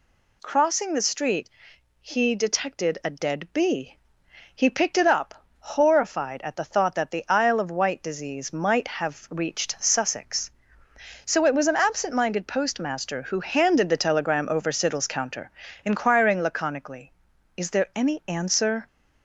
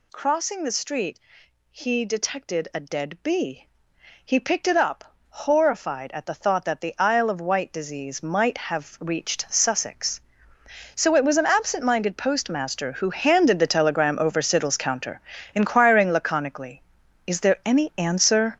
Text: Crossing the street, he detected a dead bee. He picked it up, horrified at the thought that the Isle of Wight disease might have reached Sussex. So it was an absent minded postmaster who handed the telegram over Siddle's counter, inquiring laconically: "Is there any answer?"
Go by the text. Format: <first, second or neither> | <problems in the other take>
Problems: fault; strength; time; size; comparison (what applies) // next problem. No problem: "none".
first | gets louder; strong; throughout; 9 dB